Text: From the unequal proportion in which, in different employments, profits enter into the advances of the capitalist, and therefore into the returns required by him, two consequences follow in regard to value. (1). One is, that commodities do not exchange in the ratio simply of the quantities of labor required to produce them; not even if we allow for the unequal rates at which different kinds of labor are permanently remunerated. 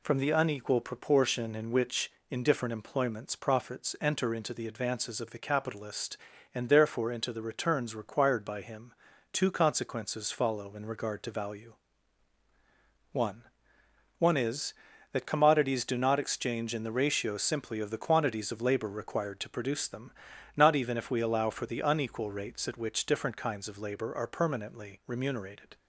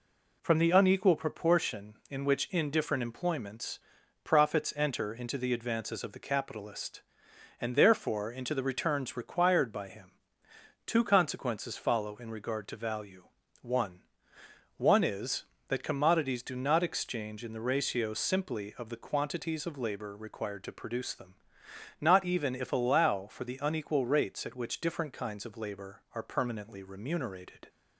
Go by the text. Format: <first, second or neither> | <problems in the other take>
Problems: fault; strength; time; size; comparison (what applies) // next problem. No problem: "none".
first | skips "we"; at 22.7 s